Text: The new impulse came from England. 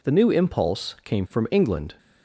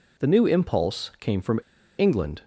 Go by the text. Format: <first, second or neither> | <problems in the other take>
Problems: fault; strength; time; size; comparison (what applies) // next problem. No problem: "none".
first | pauses between "from" and "England"; at 1.5 s; 0.38 s long